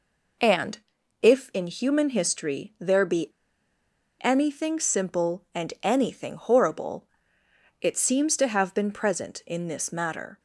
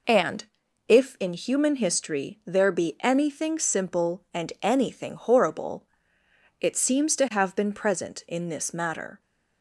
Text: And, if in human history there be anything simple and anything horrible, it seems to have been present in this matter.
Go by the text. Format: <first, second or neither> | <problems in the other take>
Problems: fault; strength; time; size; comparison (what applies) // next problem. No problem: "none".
second | pauses between "be" and "anything"; noticeable; at 3.3 s; 0.90 s long